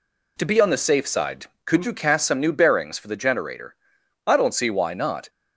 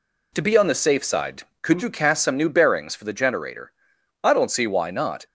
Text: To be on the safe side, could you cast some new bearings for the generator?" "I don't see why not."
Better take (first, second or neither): neither